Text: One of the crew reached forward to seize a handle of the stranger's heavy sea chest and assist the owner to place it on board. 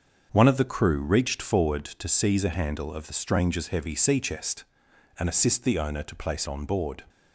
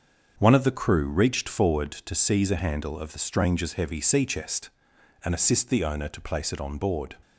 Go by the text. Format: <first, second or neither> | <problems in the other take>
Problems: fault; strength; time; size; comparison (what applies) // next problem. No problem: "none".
second | starts louder than the rest; until 1.3 s; 6.5 dB; also in the second // skips "it"; at 6.4 s